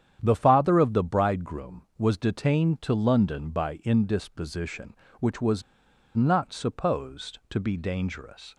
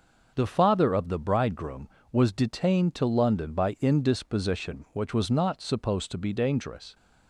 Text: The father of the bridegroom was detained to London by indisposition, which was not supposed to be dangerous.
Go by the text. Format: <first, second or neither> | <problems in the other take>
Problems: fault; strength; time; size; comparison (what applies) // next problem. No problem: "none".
second | starts louder than the rest; strong; until 1.2 s; 9.5 dB; noticeable in the second // pauses between "was" and "not"; noticeable; at 5.6 s; 0.54 s long